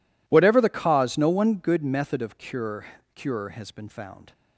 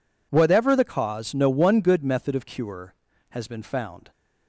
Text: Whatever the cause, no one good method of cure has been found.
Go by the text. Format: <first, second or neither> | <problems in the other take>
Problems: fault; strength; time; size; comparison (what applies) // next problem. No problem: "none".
second | says "cure" twice; at 3.1 s